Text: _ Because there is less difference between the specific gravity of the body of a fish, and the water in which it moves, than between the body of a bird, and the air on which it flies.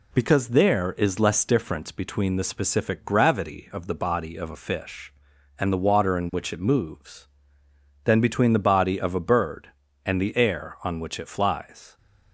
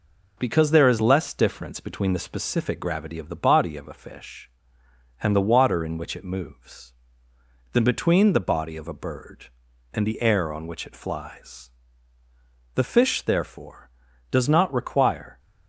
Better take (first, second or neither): first